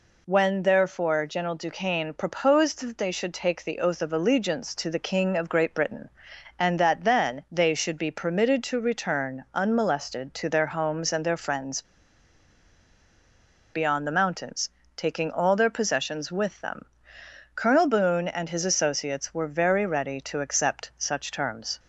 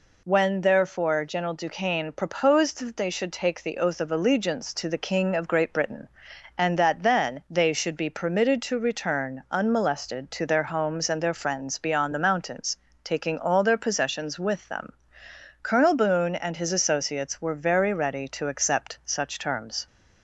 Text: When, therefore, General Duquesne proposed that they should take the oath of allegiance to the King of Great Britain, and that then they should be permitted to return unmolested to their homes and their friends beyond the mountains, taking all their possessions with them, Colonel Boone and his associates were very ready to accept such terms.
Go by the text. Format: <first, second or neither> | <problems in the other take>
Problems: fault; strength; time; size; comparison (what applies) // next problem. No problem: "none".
second | pauses between "friends" and "beyond"; strong; at 11.8 s; 1.9 s long